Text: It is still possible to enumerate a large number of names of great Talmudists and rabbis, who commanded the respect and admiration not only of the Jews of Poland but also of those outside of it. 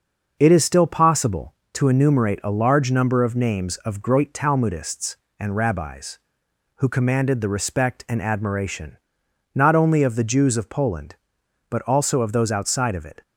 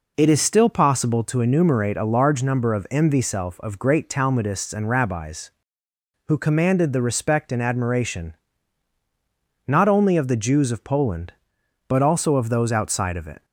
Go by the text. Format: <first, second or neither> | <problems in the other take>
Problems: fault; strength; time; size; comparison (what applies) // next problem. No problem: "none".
first | says "mvself" for "names"; at 2.8 s // pauses between "admiration" and "not"; strong; at 8.3 s; 1.3 s long; noticeable in the first